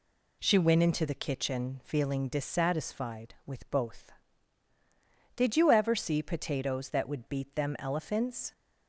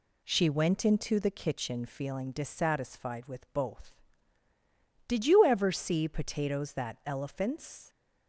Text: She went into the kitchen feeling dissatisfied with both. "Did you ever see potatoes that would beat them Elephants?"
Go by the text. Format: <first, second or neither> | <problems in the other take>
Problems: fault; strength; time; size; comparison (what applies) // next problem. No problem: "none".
first | skips "would beat them"; at 7.0 s